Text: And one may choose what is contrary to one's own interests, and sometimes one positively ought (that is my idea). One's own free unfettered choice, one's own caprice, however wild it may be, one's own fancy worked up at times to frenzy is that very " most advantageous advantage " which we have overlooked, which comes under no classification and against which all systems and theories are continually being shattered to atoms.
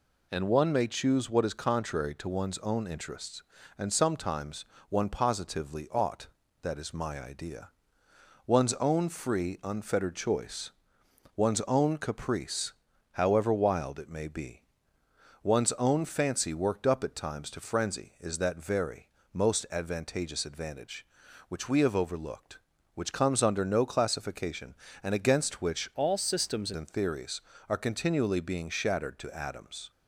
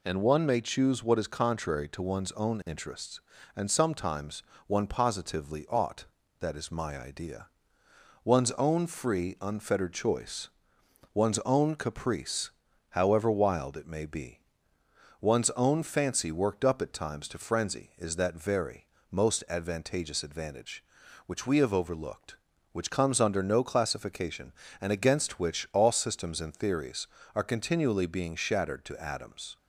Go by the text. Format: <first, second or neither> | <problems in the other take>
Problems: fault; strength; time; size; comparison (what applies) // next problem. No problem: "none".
second | pauses between "sometimes" and "one"; slight; at 4.6 s; 0.24 s long; slight in the second // changes voice from "all" to "systems"; from 25.9 to 26.7 s; 0.8 s long